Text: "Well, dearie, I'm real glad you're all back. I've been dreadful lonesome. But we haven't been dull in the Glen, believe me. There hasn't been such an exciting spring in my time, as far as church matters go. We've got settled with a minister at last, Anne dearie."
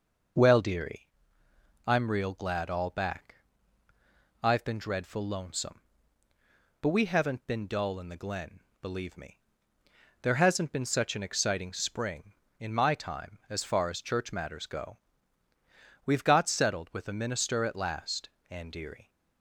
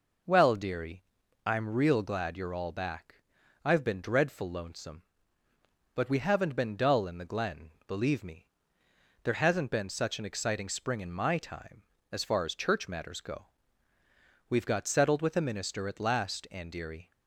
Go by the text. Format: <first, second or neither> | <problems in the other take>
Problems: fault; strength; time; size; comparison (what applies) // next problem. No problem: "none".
second | skips "you're"; at 2.6 s